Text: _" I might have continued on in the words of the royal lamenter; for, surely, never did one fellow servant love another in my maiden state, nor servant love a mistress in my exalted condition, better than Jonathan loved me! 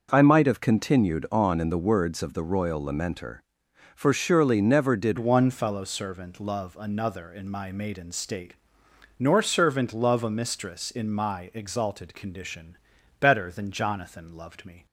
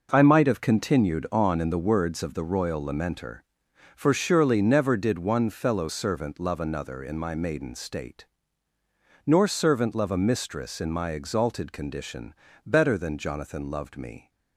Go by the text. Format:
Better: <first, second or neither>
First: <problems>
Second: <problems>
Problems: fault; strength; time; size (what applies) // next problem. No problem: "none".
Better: second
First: starts louder than the rest; noticeable; until 1.1 s; 6 dB // changes voice at "one"; from 5.1 s on; 9.7 s long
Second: none